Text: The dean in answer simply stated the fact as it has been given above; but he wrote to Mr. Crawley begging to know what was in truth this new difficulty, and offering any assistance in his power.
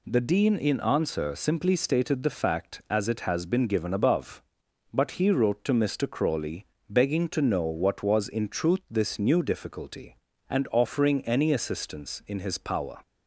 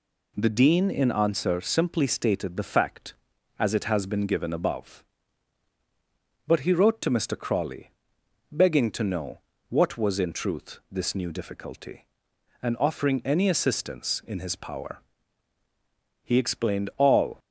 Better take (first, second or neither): first